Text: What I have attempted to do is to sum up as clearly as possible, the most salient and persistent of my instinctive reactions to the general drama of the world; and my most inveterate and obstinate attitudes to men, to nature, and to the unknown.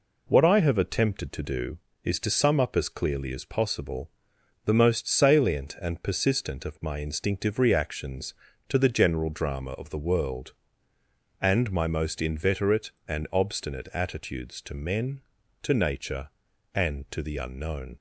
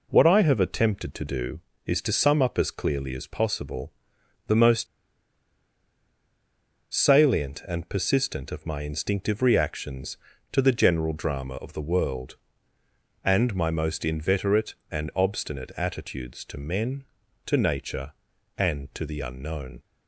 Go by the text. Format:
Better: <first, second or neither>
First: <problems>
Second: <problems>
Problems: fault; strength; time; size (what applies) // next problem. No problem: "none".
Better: first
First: none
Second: pauses between "most" and "salient"; strong; at 4.8 s; 2.0 s long